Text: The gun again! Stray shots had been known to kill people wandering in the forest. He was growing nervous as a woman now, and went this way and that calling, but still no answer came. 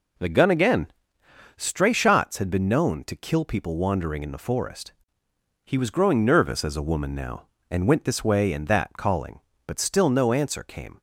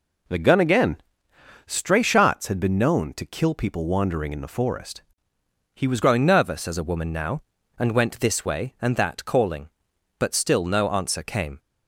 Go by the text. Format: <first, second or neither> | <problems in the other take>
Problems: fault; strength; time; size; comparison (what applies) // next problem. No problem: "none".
first | changes voice at "growing"; from 6.0 s on; 5.5 s long